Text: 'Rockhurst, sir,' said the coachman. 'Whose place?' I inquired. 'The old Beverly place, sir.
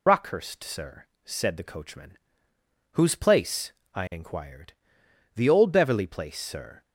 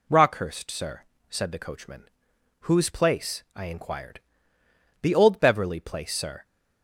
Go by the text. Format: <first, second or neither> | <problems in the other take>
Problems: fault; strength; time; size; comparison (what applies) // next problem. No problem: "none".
second | loses the start of "Rockhurst"; at 0.0 s; 50 ms